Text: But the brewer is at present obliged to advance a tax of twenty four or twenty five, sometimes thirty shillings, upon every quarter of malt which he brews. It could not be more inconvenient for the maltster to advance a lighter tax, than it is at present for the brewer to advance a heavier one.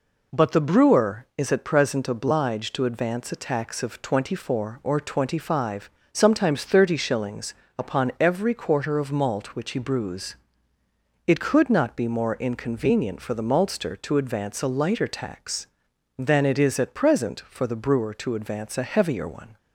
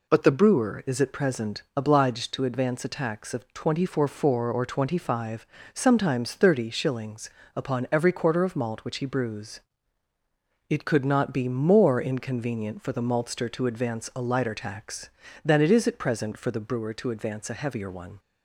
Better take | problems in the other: first | says "four" twice; at 4.0 s

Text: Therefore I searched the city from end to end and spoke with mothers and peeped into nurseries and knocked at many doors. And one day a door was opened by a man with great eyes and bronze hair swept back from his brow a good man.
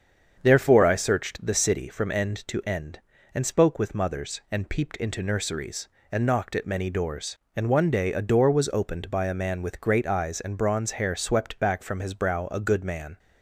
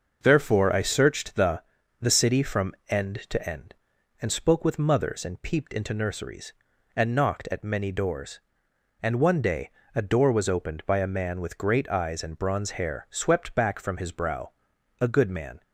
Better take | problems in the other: first | starts louder than the rest; noticeable; until 1.2 s; 6 dB; strong in the first // says "the" twice; at 1.9 s // pauses between "day" and "a"; slight; at 9.6 s; 0.24 s long // pauses between "brow" and "a"; noticeable; at 14.5 s; 0.48 s long

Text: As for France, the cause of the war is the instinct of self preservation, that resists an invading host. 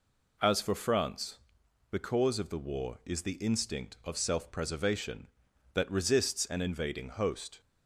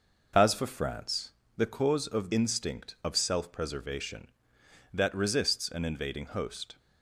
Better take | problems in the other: first | skips "the war is the"; at 2.3 s

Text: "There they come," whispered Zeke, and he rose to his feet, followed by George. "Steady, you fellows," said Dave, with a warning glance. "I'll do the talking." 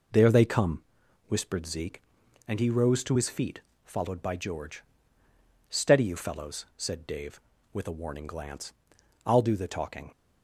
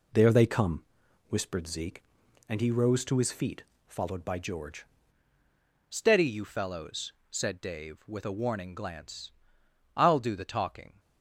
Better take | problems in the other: first | changes voice at "Steady"; from 5.8 s on; 5.1 s long

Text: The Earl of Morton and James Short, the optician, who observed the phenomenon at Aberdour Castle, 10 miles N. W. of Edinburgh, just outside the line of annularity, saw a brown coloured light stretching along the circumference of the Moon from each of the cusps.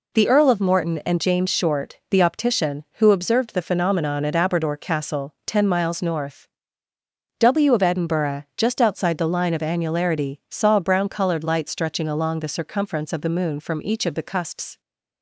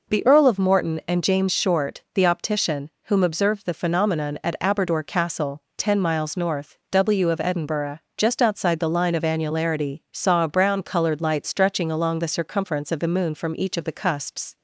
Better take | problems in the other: first | says "whom" for "who"; at 3.0 s

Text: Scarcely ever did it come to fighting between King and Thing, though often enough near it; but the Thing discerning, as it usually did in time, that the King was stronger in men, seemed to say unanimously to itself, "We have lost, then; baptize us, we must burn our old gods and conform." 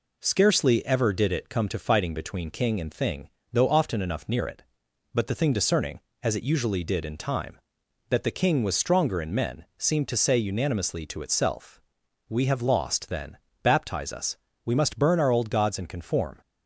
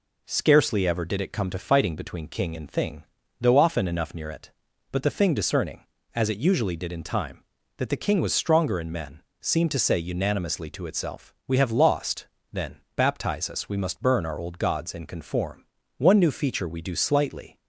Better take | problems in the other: first | goes on to say "One new feature we do slightly"; from 15.9 s on; 1.6 s long

